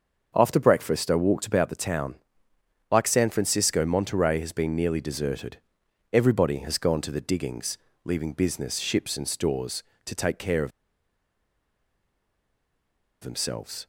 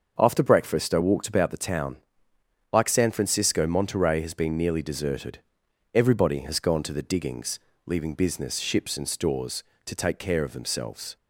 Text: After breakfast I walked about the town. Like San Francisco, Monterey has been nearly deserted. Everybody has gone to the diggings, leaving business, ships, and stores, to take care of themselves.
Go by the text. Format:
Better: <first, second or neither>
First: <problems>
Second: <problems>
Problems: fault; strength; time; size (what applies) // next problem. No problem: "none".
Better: second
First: starts louder than the rest; until 1.3 s; 6.5 dB // pauses between "of" and "themselves"; strong; at 10.7 s; 2.5 s long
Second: starts louder than the rest; until 1.2 s; 6.5 dB